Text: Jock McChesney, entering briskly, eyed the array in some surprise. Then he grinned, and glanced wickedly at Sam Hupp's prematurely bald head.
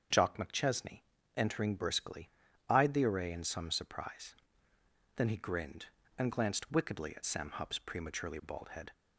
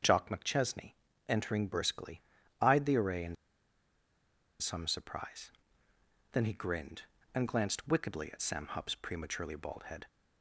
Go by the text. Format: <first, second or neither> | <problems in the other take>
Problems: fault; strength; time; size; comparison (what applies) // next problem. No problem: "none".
first | starts louder than the rest; strong; until 1.4 s; 7 dB; strong in the first // pauses between "in" and "some"; strong; at 3.3 s; 1.2 s long